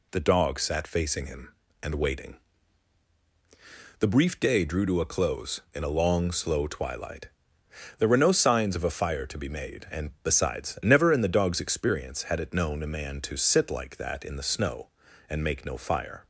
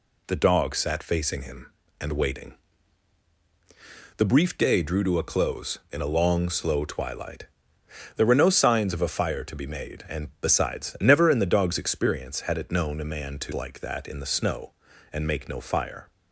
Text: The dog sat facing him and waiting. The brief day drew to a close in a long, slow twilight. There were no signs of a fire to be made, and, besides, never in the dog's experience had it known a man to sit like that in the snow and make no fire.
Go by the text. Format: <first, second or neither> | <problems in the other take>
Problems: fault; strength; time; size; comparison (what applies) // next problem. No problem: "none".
first | skips "sit"; at 13.5 s